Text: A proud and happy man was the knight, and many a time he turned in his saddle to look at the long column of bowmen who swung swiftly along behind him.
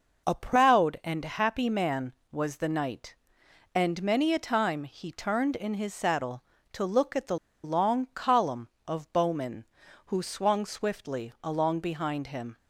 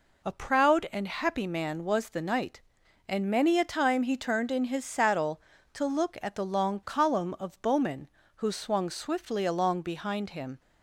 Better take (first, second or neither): second